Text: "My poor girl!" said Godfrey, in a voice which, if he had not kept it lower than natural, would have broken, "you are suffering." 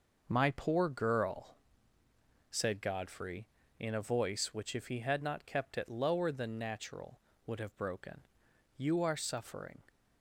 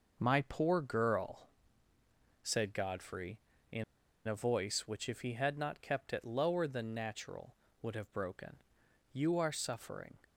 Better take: first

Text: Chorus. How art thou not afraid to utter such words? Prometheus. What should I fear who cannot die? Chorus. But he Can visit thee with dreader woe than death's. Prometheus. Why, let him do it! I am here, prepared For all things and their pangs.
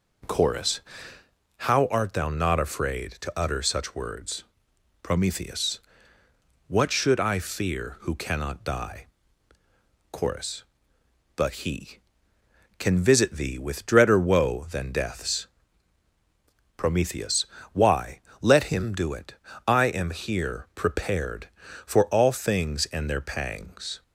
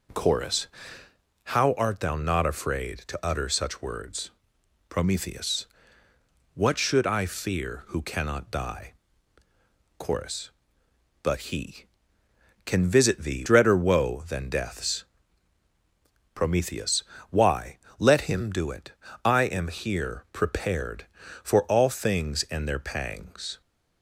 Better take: first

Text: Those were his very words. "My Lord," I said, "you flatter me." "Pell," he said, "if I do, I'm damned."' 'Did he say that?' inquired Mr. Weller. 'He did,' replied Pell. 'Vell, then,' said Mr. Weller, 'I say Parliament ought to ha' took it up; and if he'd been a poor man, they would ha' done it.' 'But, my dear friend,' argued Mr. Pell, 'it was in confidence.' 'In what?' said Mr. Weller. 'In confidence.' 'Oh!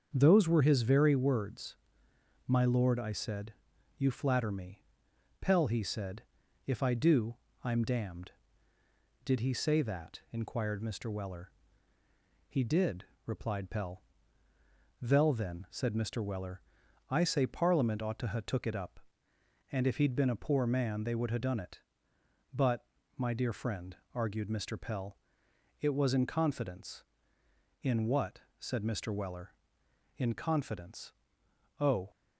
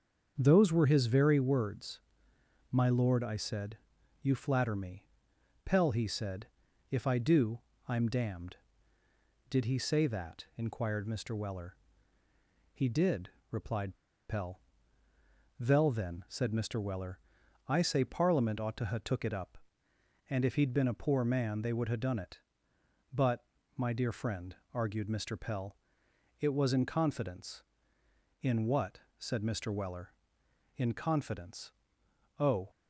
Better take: first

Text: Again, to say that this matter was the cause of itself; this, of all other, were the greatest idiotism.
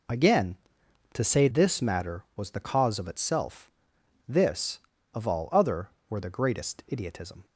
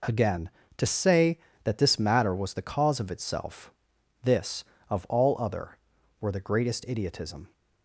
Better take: second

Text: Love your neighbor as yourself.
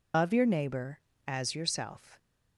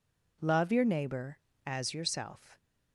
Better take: second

